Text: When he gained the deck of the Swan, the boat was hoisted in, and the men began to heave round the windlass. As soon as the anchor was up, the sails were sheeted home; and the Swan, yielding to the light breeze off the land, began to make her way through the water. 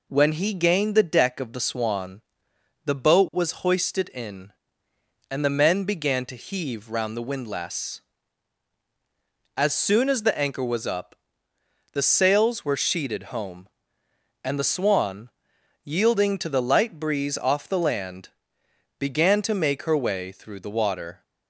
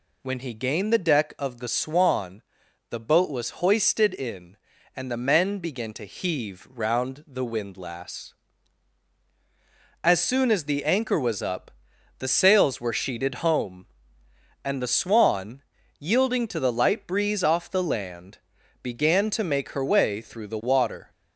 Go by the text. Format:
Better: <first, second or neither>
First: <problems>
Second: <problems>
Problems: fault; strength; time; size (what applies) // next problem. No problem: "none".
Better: neither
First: none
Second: none